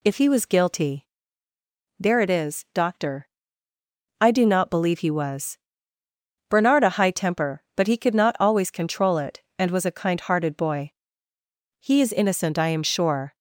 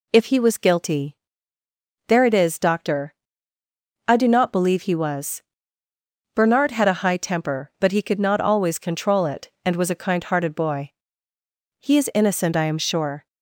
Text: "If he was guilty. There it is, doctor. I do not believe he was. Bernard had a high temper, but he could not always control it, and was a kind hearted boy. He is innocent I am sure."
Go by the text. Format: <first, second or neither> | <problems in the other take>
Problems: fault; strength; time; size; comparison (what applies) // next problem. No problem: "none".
second | skips "had"; at 6.8 s